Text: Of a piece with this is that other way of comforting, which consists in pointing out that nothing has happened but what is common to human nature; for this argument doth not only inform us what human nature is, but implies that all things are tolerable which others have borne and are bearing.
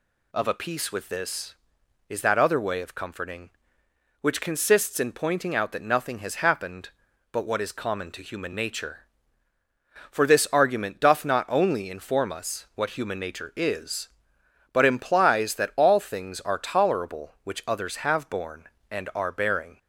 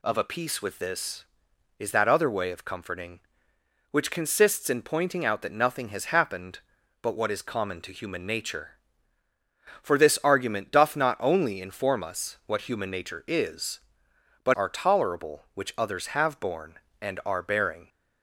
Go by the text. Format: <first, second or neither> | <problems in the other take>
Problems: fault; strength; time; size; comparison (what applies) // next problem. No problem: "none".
first | skips "implies that all things"; at 14.5 s